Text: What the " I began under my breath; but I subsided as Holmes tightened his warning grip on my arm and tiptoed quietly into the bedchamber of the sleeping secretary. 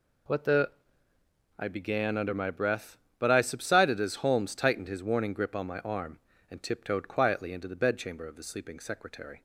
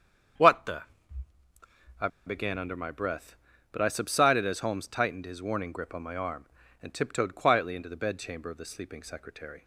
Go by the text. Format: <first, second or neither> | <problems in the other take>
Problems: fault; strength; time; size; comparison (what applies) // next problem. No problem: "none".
first | starts louder than the rest; strong; until 1.9 s; 8 dB // pauses between "I" and "began"; slight; at 2.0 s; 0.18 s long